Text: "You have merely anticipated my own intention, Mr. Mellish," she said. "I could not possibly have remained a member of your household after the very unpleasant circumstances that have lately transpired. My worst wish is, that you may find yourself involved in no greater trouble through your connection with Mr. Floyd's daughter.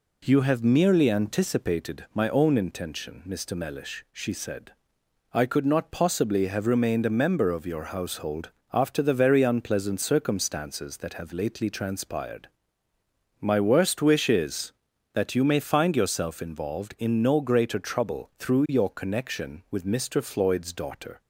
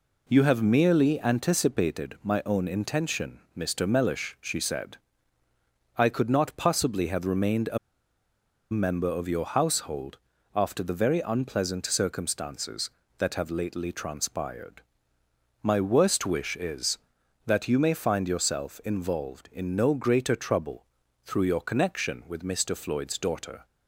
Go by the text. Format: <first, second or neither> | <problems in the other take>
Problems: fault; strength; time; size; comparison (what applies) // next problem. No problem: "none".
first | pauses between "a" and "member"; noticeable; at 7.7 s; 0.93 s long // pauses between "household" and "after"; at 10.1 s; 0.38 s long; slight in the first // pauses between "trouble" and "through"; at 20.8 s; 0.40 s long